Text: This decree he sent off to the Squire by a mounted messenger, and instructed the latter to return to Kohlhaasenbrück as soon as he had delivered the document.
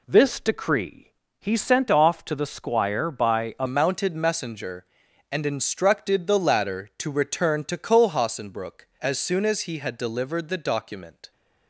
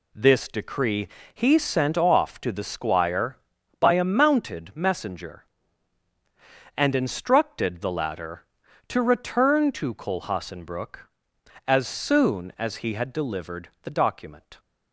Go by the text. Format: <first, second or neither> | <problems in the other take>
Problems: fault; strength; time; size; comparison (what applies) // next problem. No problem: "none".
second | pauses between "decree" and "he"; slight; at 1.1 s; 0.26 s long; slight in the second // changes voice at "mounted"; from 3.6 s on; 7.7 s long